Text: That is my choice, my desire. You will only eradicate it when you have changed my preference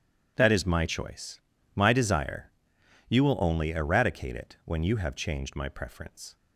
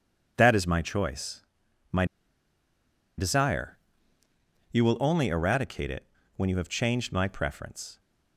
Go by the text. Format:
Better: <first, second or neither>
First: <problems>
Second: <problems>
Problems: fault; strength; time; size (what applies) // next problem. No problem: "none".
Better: first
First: none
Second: pauses between "my" and "desire"; at 2.0 s; 1.1 s long // pauses between "it" and "when"; slight; at 6.0 s; 0.32 s long